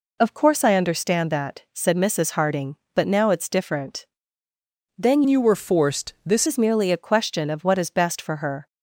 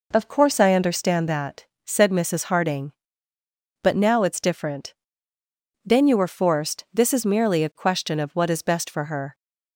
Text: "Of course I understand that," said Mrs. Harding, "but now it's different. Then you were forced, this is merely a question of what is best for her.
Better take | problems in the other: second | changes voice from "you" to "this"; from 5.2 to 6.4 s; 1.2 s long

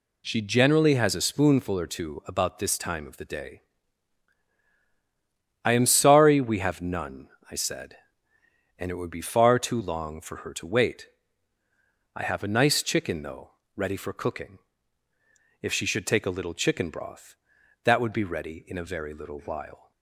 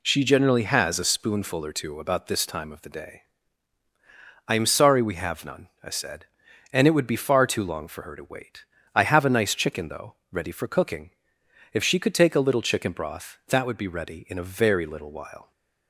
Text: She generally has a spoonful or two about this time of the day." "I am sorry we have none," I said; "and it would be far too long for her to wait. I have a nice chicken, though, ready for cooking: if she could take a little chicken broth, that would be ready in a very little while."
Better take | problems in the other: second | says "should" for "could"; at 15.8 s

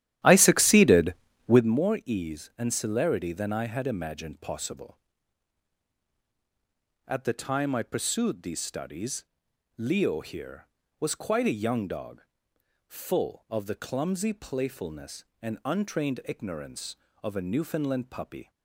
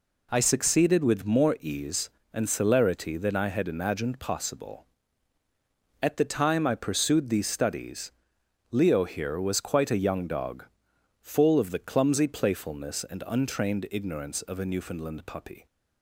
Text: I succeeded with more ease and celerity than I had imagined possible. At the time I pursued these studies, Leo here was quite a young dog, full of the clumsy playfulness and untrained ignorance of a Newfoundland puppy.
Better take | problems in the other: second | starts louder than the rest; strong; until 1.8 s; 12.5 dB

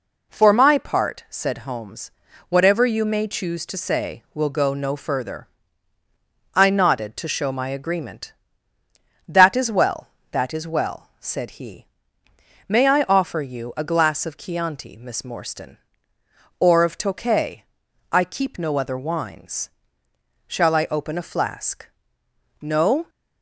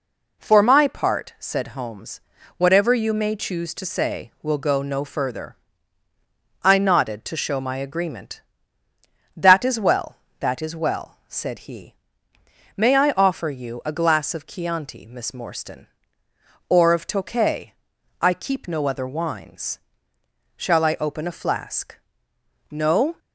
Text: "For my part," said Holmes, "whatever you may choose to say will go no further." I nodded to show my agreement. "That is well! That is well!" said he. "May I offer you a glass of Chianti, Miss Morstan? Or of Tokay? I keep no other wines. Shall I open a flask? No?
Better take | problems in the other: neither | none

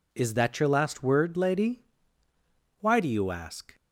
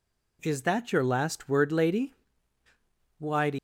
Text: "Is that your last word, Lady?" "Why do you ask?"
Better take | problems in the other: first | stops before "you ask"; at 3.5 s

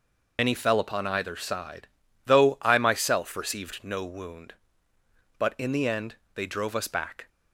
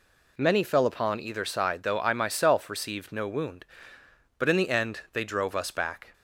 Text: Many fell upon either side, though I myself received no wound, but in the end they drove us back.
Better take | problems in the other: second | loses the start of "Many"; at 0.3 s; 110 ms // pauses between "end" and "they"; slight; at 6.1 s; 0.18 s long

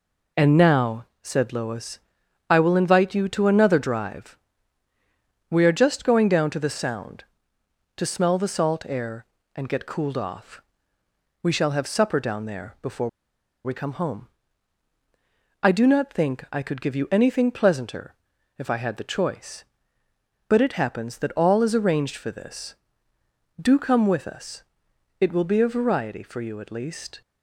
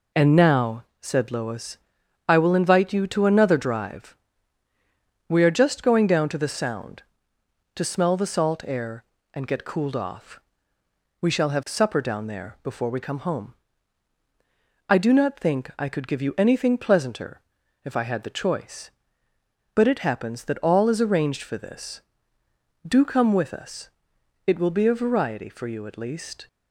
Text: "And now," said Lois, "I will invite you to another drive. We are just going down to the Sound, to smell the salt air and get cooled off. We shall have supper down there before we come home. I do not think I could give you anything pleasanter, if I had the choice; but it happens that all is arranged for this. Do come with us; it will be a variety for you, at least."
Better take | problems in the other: second | pauses between "before" and "we"; noticeable; at 13.0 s; 0.56 s long

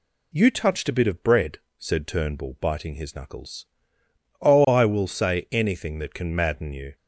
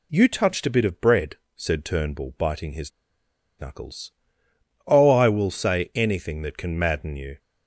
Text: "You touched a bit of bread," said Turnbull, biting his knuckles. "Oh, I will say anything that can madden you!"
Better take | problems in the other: first | pauses between "his" and "knuckles"; noticeable; at 2.9 s; 0.69 s long

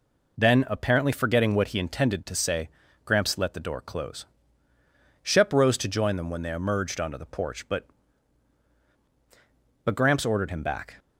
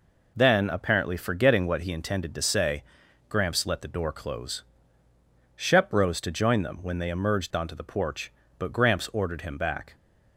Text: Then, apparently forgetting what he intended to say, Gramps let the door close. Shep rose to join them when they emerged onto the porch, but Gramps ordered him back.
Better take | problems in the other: second | says "but" twice; at 9.8 s

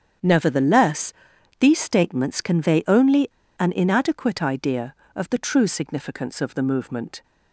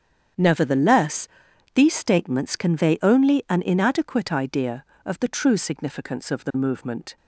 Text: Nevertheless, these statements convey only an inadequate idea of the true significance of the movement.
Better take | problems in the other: second | starts louder than the rest; strong; until 1.6 s; 8.5 dB; strong in the second // pauses between "only" and "an"; slight; at 3.2 s; 0.31 s long

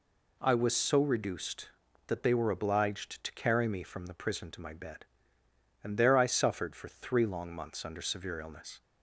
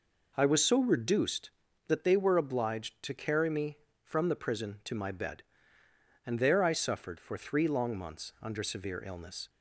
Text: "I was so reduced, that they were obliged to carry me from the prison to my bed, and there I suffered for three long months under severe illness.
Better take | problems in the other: neither | none

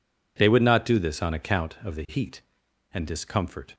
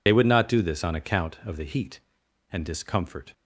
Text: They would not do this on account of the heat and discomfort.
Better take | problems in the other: first | loses the start of "They"; at 0.0 s; 60 ms

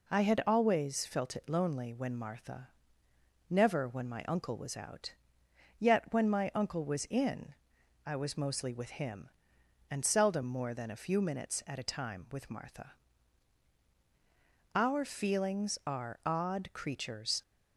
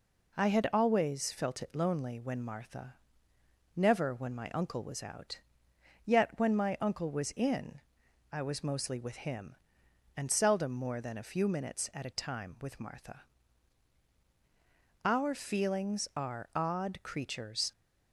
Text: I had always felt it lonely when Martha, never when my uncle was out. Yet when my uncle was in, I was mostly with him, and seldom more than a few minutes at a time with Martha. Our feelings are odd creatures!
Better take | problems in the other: neither | none

